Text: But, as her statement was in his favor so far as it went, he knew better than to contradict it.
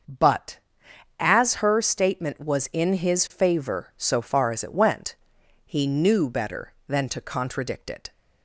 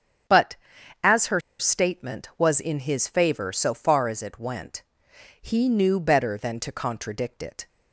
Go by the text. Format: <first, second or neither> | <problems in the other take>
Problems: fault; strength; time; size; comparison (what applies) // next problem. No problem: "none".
first | starts louder than the rest; strong; until 1.9 s; 8.5 dB; also in the first // pauses between "her" and "statement"; slight; at 1.4 s; 0.18 s long